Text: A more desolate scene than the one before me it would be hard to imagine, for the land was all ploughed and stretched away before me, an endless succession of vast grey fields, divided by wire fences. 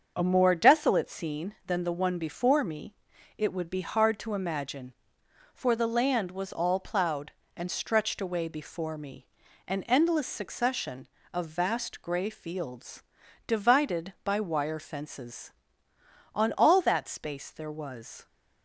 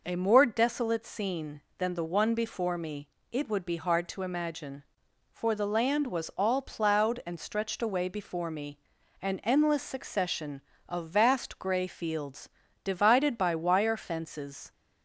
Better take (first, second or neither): second